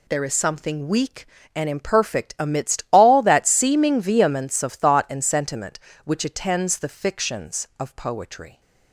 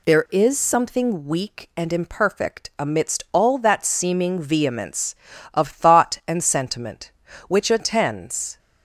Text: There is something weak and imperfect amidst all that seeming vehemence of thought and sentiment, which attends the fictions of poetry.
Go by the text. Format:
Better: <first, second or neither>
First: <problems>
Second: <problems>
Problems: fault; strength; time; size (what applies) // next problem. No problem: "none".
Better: first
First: none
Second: stops before "the fictions of poetry"; at 8.5 s